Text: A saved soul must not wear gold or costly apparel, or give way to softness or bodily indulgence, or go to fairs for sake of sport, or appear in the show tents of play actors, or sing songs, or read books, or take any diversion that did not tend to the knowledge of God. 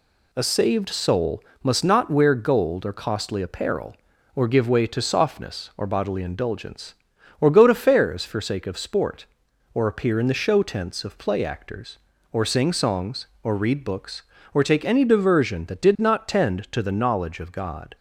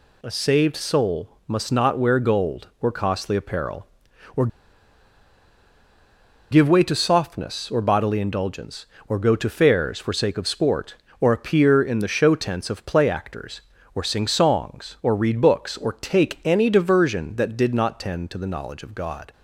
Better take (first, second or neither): first